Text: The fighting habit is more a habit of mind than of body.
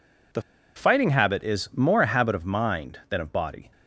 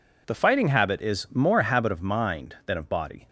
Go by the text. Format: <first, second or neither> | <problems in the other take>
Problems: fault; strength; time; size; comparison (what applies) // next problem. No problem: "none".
second | pauses between "The" and "fighting"; slight; at 0.4 s; 0.34 s long